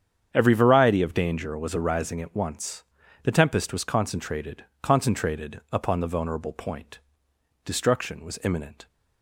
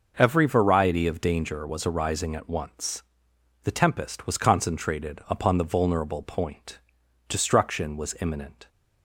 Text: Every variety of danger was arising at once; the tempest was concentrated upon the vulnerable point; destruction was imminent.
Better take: second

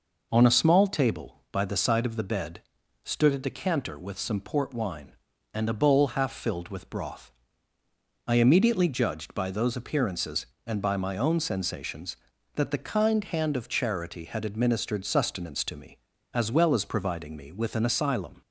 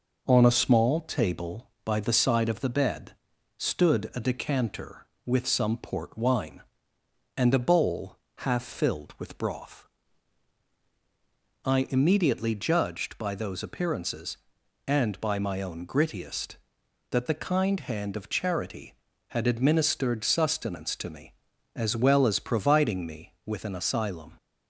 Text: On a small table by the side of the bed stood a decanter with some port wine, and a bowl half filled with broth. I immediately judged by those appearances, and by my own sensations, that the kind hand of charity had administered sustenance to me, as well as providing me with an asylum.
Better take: first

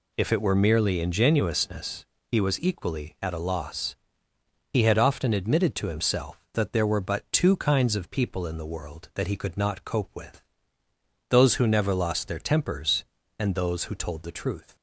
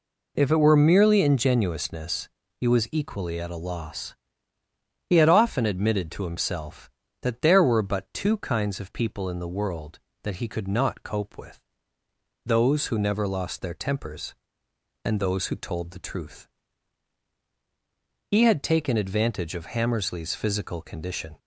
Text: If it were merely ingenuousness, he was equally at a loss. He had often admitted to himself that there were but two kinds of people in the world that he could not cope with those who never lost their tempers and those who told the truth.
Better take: first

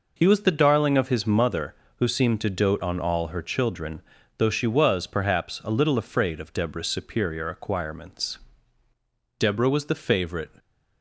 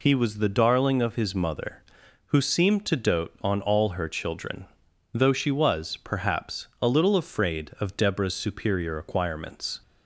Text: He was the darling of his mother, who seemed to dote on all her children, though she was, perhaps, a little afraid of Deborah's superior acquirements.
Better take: second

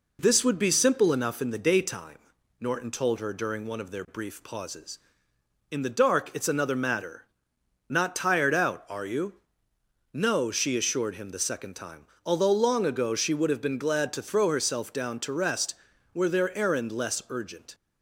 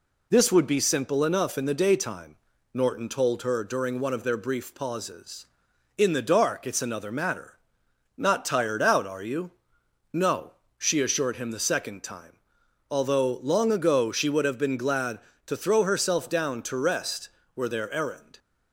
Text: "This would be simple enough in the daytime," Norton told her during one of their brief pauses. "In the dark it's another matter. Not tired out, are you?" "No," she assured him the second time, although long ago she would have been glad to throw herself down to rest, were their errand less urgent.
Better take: first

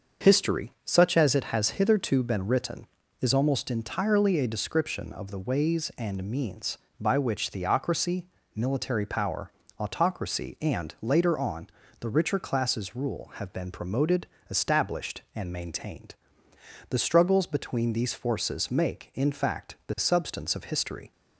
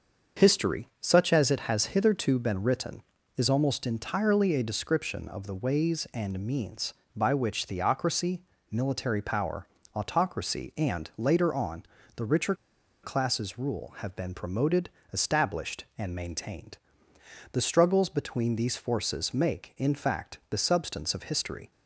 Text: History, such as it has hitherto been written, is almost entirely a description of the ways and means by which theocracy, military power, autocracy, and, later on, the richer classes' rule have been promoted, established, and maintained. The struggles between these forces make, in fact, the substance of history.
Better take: first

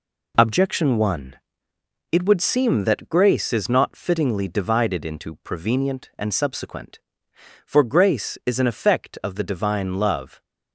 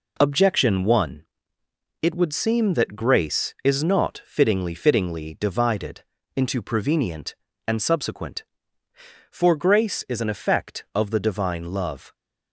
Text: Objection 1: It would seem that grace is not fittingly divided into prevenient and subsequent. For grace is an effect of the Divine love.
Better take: first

